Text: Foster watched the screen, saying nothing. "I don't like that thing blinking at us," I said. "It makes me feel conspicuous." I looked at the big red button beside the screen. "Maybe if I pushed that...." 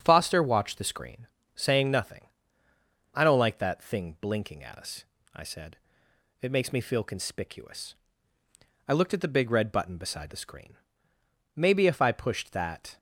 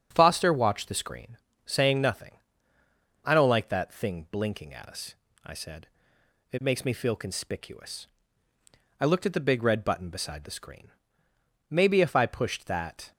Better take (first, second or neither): neither